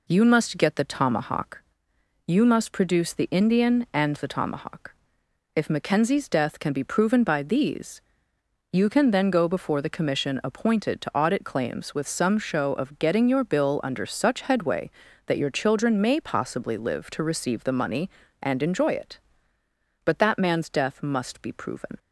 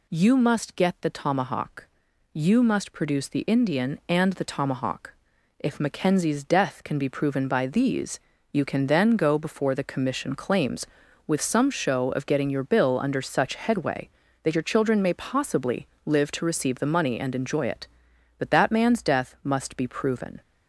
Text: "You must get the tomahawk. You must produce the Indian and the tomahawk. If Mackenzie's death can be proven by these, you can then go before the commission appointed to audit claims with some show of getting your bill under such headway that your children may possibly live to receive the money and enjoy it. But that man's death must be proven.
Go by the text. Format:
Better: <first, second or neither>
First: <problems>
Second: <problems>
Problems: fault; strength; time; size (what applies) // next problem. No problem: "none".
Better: first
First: none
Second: skips "appointed to audit"; at 10.3 s // pauses between "possibly" and "live"; slight; at 15.8 s; 0.16 s long